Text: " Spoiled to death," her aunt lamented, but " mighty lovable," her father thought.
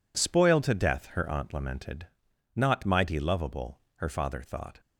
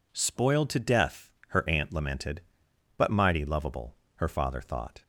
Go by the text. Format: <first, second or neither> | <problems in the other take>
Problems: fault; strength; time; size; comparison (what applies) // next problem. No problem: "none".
second | says "not" for "but"; at 2.5 s